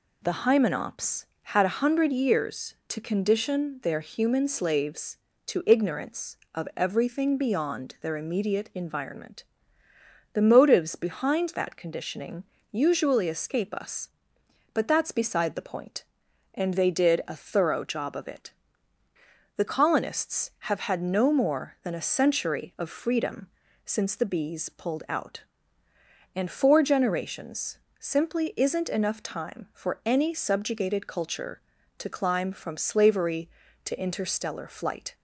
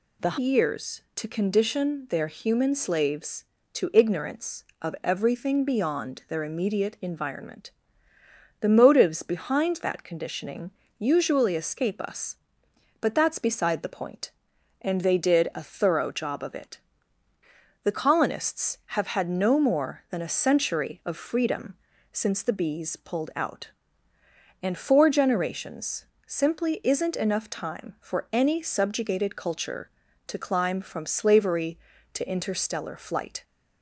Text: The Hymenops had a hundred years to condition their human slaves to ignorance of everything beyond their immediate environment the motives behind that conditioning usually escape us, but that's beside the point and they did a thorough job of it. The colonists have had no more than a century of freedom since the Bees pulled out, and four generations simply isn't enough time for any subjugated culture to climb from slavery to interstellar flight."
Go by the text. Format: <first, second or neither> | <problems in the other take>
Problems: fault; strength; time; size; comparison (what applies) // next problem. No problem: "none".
first | skips "Hymenops had a hundred"; at 0.3 s // pauses between "environment" and "the"; noticeable; at 7.6 s; 0.90 s long; noticeable in the first // pauses between "conditioning" and "usually"; slight; at 10.6 s; 0.28 s long; slight in the first // pauses between "freedom" and "since"; at 21.7 s; 0.38 s long; also in the first // pauses between "generations" and "simply"; slight; at 26.0 s; 0.22 s long; slight in the first